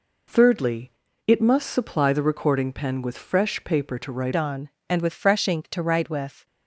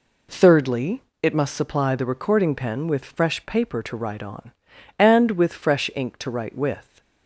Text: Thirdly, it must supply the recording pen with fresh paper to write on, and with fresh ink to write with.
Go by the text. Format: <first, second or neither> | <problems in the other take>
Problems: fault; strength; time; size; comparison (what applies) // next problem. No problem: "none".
second | changes voice at "on"; from 4.3 s on; 2.1 s long